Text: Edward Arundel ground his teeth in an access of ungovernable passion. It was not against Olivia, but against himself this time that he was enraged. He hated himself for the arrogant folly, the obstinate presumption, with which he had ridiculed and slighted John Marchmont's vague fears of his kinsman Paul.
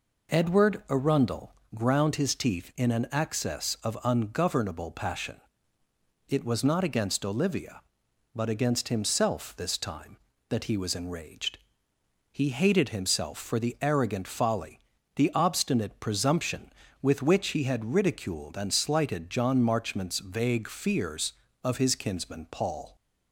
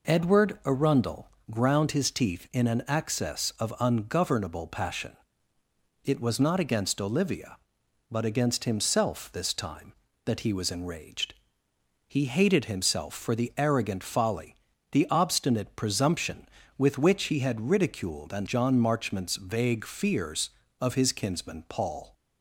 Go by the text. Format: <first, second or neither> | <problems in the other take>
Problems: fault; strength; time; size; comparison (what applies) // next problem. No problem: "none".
first | pauses between "Arundel" and "ground"; slight; at 1.2 s; 0.20 s long; slight in the first // skips "slighted"; at 18.4 s